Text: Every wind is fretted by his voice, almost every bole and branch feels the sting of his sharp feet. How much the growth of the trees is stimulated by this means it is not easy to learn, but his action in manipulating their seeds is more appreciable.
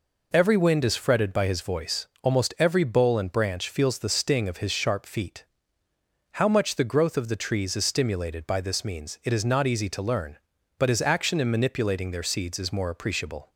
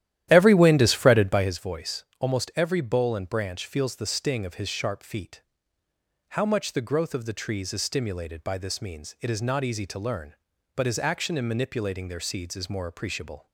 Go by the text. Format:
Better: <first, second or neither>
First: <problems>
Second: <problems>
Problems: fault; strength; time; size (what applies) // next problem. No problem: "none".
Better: first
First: none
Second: starts louder than the rest; strong; until 1.6 s; 12.5 dB